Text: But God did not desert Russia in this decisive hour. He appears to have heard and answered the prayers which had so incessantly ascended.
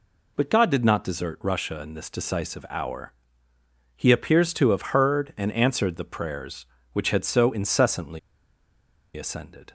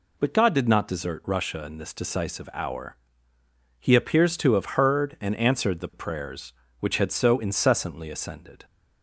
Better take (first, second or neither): second